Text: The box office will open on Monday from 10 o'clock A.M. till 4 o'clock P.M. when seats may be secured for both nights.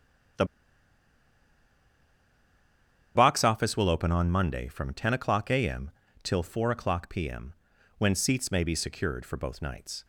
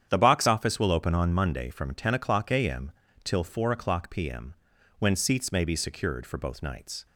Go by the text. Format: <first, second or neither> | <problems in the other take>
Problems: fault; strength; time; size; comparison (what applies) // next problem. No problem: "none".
second | starts louder than the rest; strong; until 4.0 s; 9 dB; strong in the second // pauses between "The" and "box"; strong; at 0.4 s; 2.7 s long